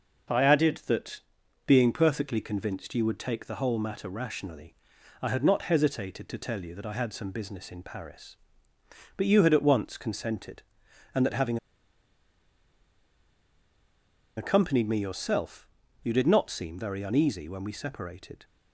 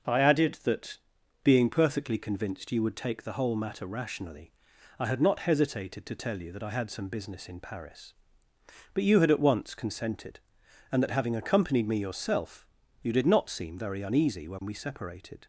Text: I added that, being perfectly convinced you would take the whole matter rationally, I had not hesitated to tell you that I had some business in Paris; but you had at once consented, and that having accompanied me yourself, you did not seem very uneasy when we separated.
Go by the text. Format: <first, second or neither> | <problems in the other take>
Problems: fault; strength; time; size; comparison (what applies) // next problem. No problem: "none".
second | starts louder than the rest; noticeable; until 1.8 s; 6 dB; noticeable in the second // pauses between "having" and "accompanied"; strong; at 11.5 s; 2.8 s long